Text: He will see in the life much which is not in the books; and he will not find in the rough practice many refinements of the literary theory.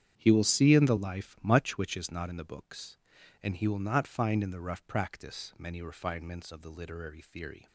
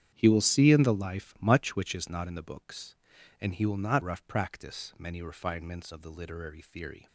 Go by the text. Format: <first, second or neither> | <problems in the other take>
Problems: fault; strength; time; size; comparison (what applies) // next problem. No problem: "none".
first | starts louder than the rest; strong; until 1.1 s; 9.5 dB; strong in the first // skips "find in the"; at 4.0 s